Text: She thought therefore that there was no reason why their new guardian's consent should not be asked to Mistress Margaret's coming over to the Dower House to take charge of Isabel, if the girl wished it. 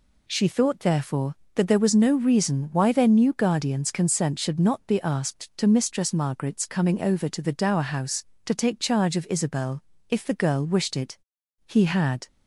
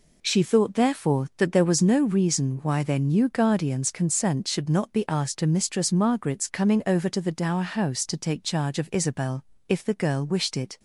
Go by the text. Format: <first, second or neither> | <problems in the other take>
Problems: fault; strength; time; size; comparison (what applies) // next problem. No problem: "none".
second | goes on to say "He had"; noticeable; from 11.6 s on; 0.62 s long